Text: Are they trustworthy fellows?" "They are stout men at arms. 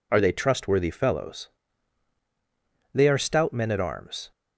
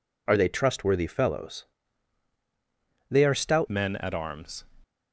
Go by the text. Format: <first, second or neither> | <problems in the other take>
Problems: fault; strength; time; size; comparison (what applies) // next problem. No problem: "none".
first | changes voice at "men"; from 3.6 s on; 1.0 s long